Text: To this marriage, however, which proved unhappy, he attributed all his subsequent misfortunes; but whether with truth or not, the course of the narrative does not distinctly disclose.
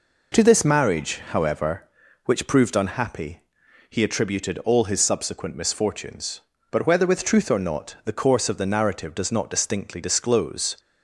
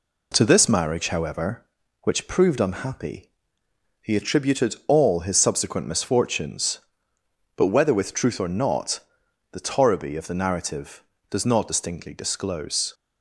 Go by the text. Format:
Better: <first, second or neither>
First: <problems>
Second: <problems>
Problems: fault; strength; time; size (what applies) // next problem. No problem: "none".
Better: first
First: none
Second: says "torriby" for "course"; at 9.6 s